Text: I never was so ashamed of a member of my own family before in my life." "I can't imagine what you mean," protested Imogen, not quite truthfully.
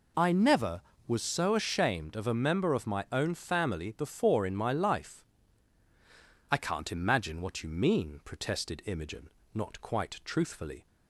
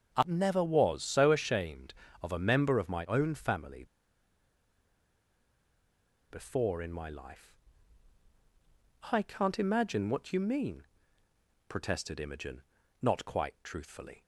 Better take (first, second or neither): first